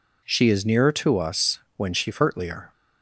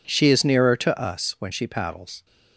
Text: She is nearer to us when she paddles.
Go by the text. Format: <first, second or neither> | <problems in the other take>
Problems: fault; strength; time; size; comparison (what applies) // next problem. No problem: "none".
second | pauses between "us" and "when"; slight; at 1.5 s; 0.18 s long // says "furtlier" for "paddles"; at 2.1 s